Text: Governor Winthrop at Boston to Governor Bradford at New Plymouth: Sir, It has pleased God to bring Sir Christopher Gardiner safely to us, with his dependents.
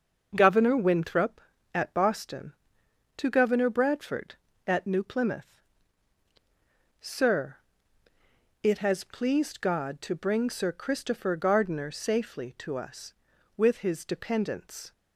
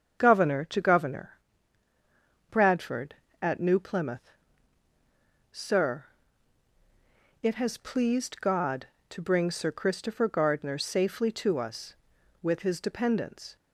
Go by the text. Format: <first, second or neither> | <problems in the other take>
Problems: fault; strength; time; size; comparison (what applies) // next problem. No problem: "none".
first | starts louder than the rest; strong; until 1.2 s; 7.5 dB; also in the first // skips "Winthrop at Boston"; at 0.6 s // pauses between "Governor" and "Bradford"; at 1.3 s; 1.2 s long